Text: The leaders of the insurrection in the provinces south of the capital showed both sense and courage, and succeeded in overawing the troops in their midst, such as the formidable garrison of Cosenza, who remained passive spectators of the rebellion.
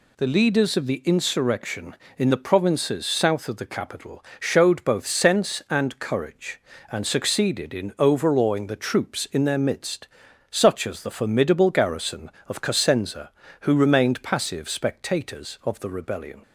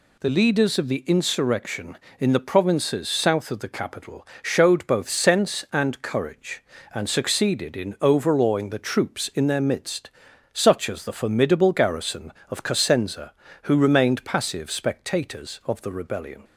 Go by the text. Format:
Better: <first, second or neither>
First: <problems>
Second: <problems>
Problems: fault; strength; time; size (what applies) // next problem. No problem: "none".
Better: neither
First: pauses between "capital" and "showed"; slight; at 4.2 s; 0.18 s long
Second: pauses between "capital" and "showed"; slight; at 4.2 s; 0.18 s long